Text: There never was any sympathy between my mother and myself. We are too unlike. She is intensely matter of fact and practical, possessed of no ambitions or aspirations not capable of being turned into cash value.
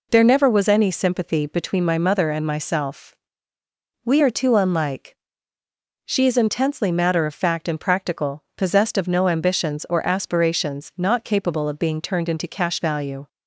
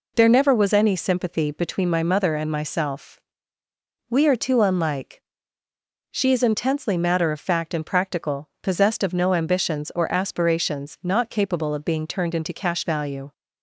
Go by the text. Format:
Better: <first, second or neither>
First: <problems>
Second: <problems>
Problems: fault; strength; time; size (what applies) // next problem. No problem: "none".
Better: neither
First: none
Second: none